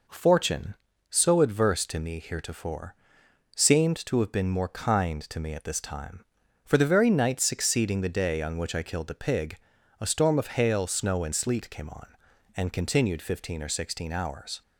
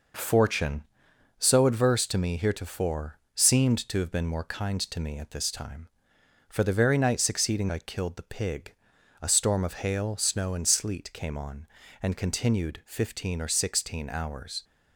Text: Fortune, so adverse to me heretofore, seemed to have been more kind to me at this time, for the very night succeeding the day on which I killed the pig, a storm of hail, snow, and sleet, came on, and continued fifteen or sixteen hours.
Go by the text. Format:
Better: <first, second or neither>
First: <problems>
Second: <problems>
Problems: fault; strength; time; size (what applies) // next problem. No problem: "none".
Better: first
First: none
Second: skips "the day on which"; at 7.6 s